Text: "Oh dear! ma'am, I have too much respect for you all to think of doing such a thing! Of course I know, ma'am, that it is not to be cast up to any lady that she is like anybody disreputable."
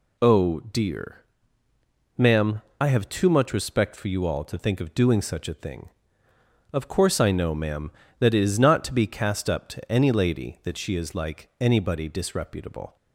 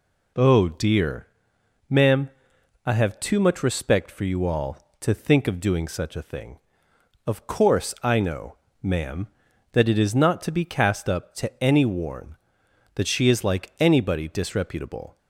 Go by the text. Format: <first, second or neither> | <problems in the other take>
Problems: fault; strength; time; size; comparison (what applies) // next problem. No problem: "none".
first | says "worn" for "lady"; at 11.8 s